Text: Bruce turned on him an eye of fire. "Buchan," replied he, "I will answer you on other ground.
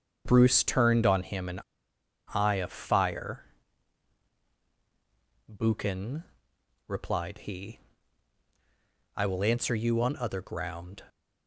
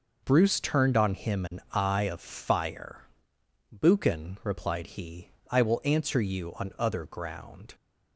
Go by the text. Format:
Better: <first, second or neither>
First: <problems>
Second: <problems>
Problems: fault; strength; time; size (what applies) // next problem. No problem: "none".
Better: second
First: starts louder than the rest; until 1.2 s; 7 dB // pauses between "an" and "eye"; noticeable; at 1.6 s; 0.74 s long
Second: none